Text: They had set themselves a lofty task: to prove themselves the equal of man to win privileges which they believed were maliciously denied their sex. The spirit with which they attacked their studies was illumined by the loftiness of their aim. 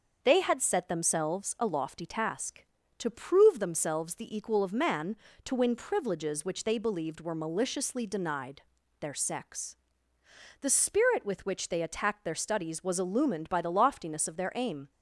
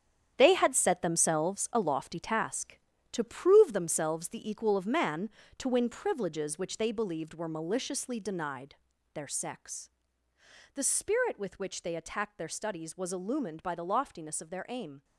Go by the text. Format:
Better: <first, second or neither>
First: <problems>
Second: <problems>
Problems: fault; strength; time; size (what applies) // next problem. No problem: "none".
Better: first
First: starts louder than the rest; noticeable; until 1.2 s; 6 dB // pauses between "denied" and "their"; at 8.6 s; 0.40 s long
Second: gets quieter; strong; throughout; 10 dB // starts louder than the rest; strong; until 1.3 s; 9 dB // pauses between "denied" and "their"; at 8.7 s; 0.40 s long